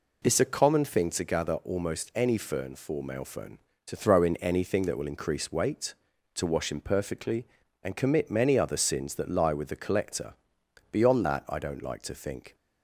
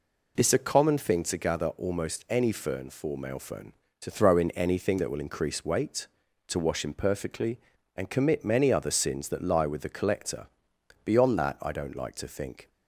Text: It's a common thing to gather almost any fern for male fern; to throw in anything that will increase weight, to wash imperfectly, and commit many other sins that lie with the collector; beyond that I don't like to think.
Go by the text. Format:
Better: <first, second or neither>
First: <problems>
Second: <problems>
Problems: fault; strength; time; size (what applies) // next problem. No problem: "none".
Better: neither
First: none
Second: none